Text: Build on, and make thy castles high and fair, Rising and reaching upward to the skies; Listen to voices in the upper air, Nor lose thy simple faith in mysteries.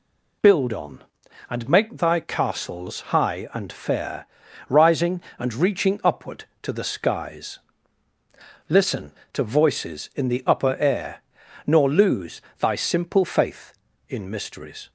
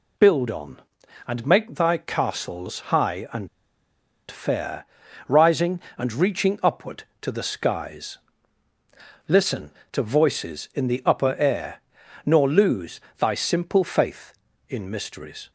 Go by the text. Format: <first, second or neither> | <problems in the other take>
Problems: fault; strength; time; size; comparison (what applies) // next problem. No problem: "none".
first | pauses between "and" and "fair"; noticeable; at 3.4 s; 0.82 s long // pauses between "lose" and "thy"; slight; at 12.9 s; 0.20 s long; slight in the first